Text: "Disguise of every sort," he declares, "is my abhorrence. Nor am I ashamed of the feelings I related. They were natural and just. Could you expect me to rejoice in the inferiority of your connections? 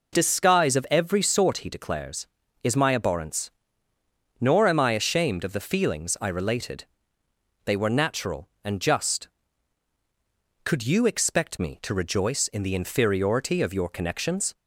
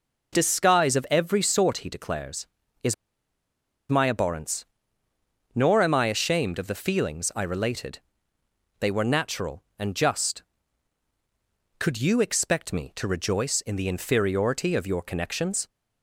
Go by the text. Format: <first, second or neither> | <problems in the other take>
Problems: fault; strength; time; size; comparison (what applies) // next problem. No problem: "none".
first | pauses between "is" and "my"; noticeable; at 2.9 s; 0.95 s long